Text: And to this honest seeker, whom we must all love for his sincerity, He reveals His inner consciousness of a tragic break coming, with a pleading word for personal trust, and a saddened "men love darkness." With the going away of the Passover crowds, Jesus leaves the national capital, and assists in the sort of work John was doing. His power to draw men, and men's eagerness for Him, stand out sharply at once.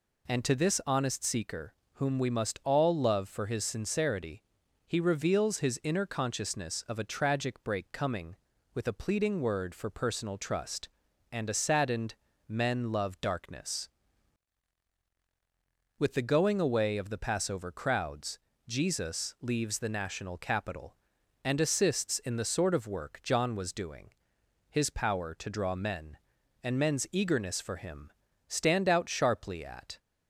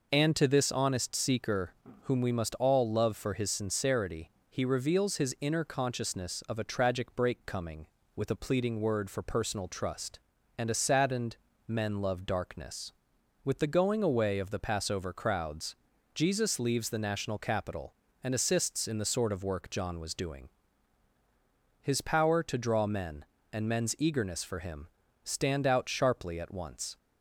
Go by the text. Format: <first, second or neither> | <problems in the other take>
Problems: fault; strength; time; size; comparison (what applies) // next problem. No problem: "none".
second | pauses between "saddened" and "men"; slight; at 12.1 s; 0.32 s long; slight in the second // stops before "once"; at 29.9 s